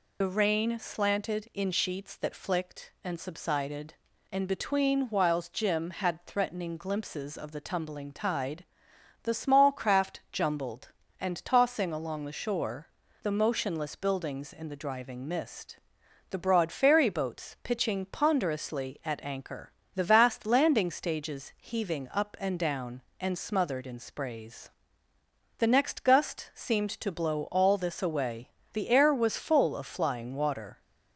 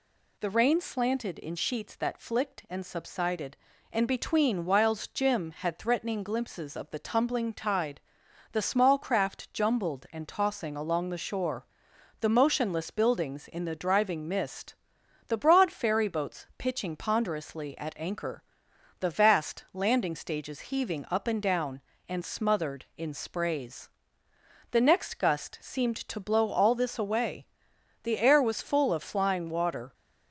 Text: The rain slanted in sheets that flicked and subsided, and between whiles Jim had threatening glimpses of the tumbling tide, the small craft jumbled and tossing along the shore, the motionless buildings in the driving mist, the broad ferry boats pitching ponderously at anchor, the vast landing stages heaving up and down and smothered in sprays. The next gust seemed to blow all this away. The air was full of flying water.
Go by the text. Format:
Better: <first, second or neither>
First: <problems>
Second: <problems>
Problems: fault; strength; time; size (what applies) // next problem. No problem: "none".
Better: second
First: loses the start of "The"; at 0.2 s; 40 ms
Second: none